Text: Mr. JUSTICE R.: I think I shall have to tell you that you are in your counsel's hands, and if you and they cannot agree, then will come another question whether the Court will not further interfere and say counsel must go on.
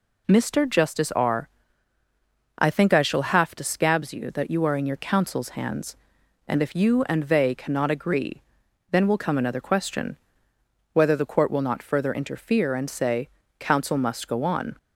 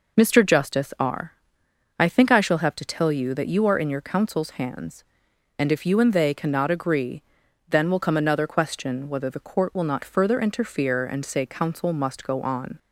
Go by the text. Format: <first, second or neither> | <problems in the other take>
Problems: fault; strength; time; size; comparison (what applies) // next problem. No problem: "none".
second | says "scabs" for "tell"; at 3.6 s // pauses between "question" and "whether"; noticeable; at 10.1 s; 0.78 s long // pauses between "say" and "counsel"; slight; at 13.2 s; 0.32 s long